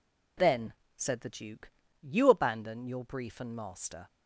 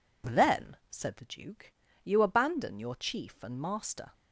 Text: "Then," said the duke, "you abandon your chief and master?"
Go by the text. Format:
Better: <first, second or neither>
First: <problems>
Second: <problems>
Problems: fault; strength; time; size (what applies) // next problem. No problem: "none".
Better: second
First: says "brief" for "chief"; at 3.0 s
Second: none